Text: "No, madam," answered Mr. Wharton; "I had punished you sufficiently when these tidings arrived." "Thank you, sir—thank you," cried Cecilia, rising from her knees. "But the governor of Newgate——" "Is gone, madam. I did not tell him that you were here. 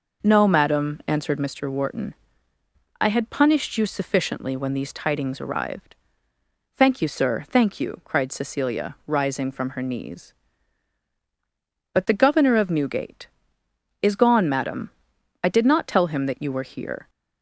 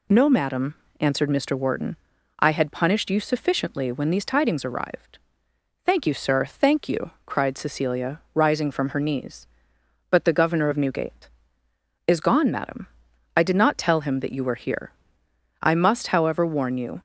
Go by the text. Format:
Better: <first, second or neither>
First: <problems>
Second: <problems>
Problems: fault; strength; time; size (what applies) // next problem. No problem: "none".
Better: first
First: none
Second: goes on to say "I must however warn you"; from 15.6 s on; 1.4 s long